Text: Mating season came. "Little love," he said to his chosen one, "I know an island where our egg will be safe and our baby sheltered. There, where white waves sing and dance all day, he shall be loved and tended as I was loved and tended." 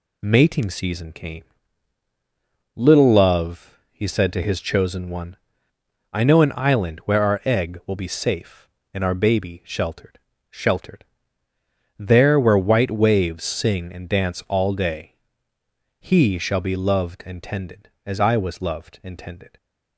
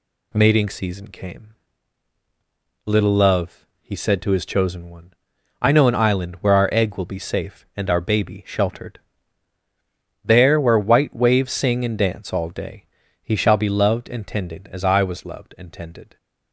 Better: second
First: says "sheltered" twice; at 10.5 s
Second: none

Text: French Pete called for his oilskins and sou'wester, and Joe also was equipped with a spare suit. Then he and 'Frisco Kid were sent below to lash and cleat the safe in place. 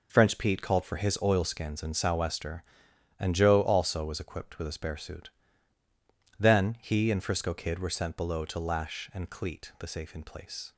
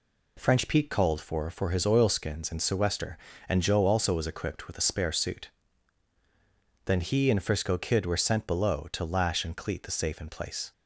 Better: first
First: none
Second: says "for" twice; at 1.4 s

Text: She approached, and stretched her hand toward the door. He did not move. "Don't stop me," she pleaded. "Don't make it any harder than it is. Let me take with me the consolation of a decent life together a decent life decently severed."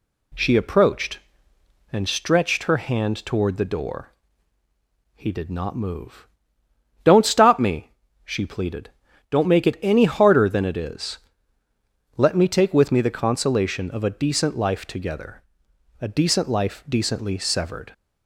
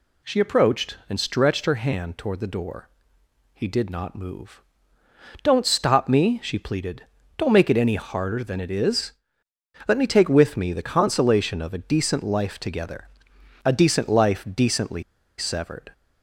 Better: first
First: pauses between "together" and "a"; noticeable; at 15.4 s; 0.61 s long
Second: pauses between "together" and "a"; noticeable; at 13.0 s; 0.58 s long // pauses between "decently" and "severed"; at 15.0 s; 0.36 s long

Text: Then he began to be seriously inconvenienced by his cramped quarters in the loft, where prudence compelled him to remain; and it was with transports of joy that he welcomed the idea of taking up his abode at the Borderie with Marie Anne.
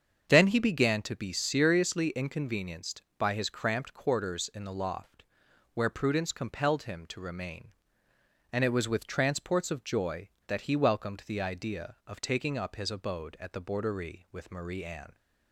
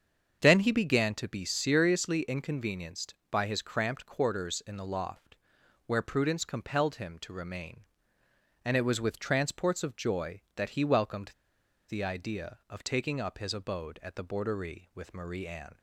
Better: first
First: starts louder than the rest; strong; until 1.3 s; 7 dB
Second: starts louder than the rest; strong; until 1.4 s; 7 dB // pauses between "welcomed" and "the"; noticeable; at 11.3 s; 0.57 s long

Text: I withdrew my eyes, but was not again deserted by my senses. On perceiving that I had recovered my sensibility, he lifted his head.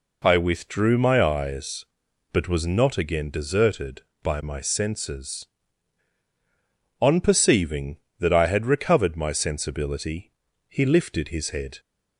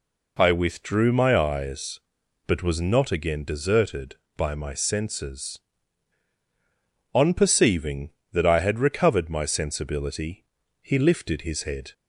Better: neither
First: none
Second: none

